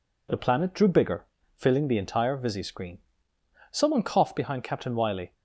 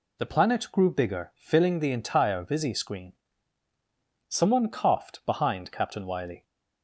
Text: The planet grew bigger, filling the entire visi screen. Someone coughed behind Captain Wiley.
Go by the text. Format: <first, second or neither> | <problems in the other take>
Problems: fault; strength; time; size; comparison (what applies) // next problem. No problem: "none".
second | says "drew" for "grew"; at 0.7 s